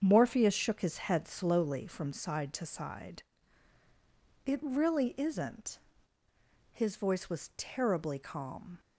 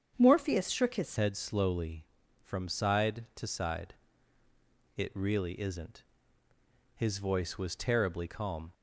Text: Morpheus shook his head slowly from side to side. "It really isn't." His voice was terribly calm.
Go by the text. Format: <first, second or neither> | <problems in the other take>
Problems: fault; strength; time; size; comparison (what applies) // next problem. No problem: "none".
first | starts louder than the rest; strong; until 1.1 s; 7.5 dB; strong in the first // changes voice at "head"; from 1.1 s on; 7.6 s long